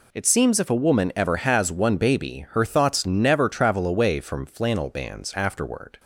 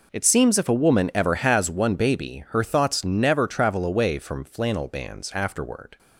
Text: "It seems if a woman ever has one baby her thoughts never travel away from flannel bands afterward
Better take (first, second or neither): first